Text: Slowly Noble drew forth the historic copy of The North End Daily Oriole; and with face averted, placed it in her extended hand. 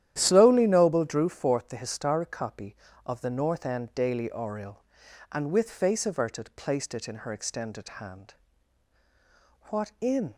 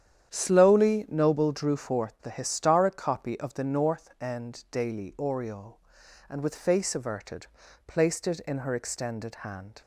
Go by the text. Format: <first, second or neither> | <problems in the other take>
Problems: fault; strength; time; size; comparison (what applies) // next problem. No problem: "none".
second | starts louder than the rest; strong; until 1.1 s; 11 dB; strong in the second // goes on to say "What in"; noticeable; from 9.6 s on; 0.66 s long